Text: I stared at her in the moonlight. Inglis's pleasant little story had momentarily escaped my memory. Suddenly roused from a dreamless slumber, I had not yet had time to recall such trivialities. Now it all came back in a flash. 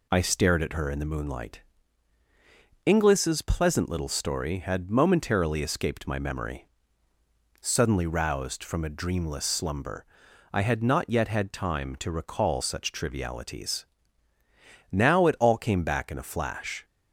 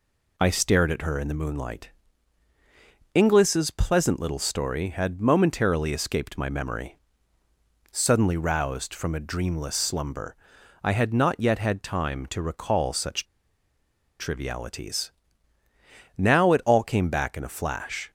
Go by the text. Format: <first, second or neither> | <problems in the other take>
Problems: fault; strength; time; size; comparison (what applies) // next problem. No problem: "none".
first | pauses between "such" and "trivialities"; noticeable; at 13.2 s; 0.95 s long